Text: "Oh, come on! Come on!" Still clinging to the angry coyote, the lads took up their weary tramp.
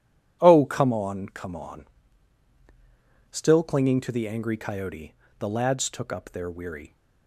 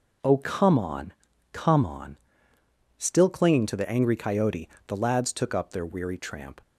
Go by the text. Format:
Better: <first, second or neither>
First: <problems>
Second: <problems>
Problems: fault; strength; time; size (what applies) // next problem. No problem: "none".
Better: second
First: stops before "tramp"; at 6.9 s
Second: none